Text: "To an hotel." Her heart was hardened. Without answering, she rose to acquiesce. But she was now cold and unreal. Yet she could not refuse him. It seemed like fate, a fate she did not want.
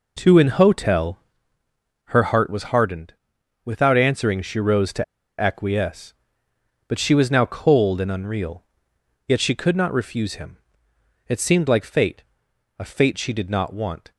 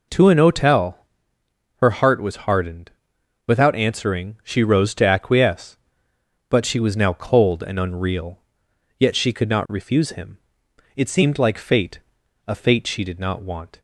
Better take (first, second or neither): second